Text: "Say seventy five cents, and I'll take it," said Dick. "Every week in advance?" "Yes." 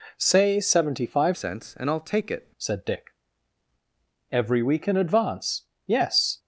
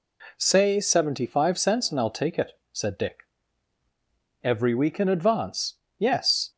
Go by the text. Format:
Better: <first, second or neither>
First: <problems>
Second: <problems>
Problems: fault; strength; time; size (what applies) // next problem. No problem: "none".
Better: second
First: changes voice from "cents" to "it"; from 1.3 to 2.4 s; 1.1 s long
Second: none